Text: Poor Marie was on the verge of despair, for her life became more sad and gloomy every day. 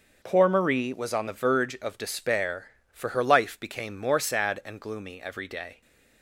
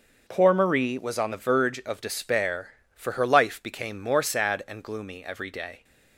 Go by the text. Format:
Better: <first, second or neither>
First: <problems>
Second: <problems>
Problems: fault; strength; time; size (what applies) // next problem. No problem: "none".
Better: neither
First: starts louder than the rest; noticeable; until 1.2 s; 6 dB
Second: starts louder than the rest; noticeable; until 1.2 s; 6 dB